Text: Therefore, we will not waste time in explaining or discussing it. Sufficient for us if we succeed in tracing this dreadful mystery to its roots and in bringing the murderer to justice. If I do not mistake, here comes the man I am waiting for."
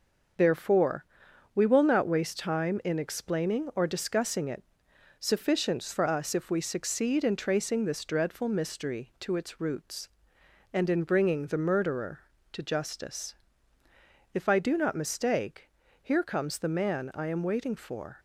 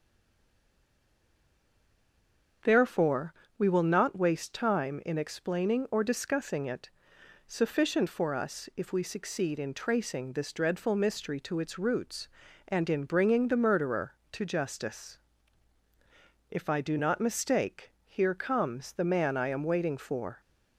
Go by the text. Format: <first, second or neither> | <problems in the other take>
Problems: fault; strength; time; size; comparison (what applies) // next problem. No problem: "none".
first | stays silent before the first word; strong; until 2.6 s; 2.6 s long // starts louder than the rest; until 3.8 s; 6.5 dB; also in the first